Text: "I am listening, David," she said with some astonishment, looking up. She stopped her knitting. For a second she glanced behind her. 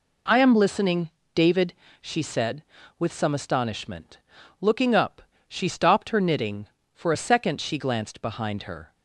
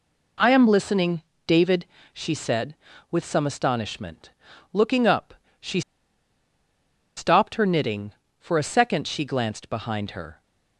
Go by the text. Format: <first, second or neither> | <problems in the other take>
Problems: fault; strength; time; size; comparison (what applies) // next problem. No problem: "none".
first | pauses between "She" and "stopped"; strong; at 5.8 s; 1.3 s long